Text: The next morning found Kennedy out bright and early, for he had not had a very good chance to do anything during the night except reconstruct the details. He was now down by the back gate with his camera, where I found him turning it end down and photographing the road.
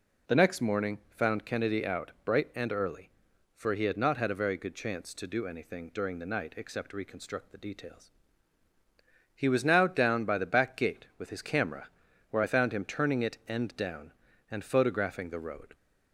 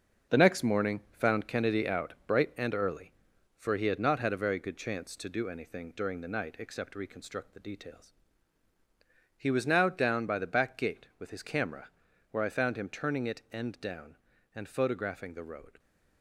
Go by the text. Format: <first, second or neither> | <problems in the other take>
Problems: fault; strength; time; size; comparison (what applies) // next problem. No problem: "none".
first | gets quieter; strong; throughout; 8 dB